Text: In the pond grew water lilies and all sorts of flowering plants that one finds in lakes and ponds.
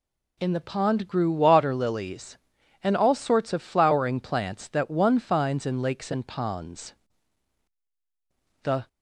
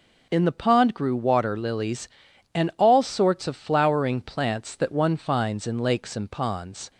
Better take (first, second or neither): second